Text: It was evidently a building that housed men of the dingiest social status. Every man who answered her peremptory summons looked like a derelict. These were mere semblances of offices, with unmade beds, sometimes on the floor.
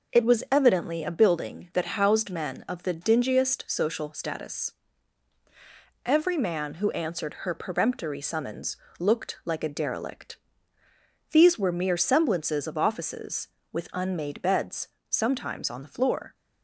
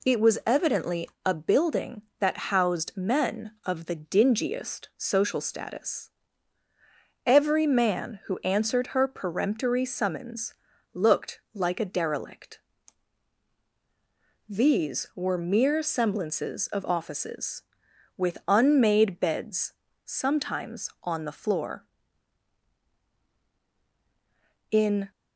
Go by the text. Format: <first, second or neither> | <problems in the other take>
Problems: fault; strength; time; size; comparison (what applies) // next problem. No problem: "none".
first | pauses between "evidently" and "a"; slight; at 1.0 s; 0.18 s long // pauses between "summons" and "looked"; at 10.5 s; 0.40 s long; slight in the first // goes on to say "In"; slight; from 24.7 s on; 0.40 s long